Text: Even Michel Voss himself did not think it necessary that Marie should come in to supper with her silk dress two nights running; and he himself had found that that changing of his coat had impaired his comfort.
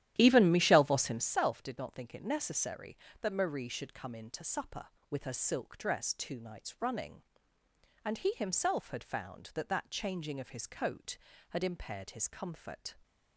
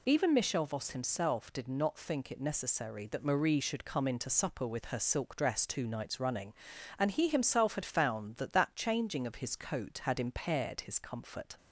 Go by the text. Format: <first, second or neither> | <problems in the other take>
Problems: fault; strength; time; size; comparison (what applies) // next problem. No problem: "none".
second | starts louder than the rest; strong; until 1.4 s; 12.5 dB